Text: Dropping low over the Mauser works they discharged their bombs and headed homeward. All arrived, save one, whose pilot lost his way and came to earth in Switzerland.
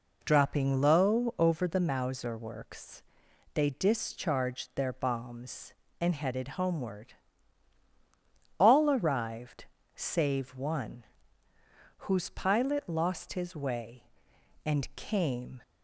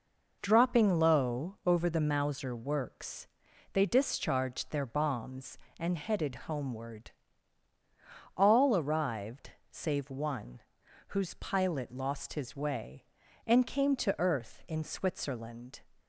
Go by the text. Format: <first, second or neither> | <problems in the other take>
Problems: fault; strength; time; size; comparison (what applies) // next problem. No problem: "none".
second | pauses between "works" and "they"; noticeable; at 3.0 s; 0.52 s long; noticeable in the second // stops before "to earth in Switzerland"; at 15.6 s